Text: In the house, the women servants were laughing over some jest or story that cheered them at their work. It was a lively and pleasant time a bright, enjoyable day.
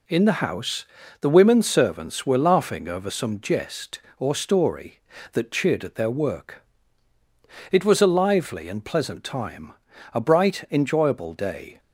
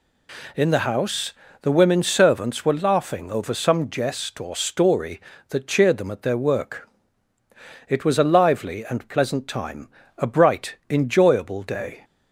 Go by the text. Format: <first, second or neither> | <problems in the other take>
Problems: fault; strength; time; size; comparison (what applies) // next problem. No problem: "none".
second | skips "them"; at 5.8 s // pauses between "time" and "a"; at 9.7 s; 0.38 s long; slight in the second